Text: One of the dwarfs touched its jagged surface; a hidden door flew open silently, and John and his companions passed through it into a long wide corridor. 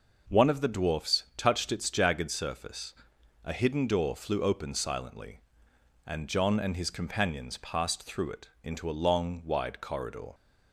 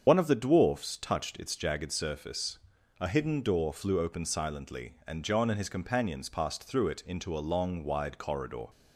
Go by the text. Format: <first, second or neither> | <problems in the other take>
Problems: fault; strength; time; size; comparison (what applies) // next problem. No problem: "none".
first | loses the start of "One"; at 0.0 s; 50 ms // starts louder than the rest; strong; until 1.0 s; 7 dB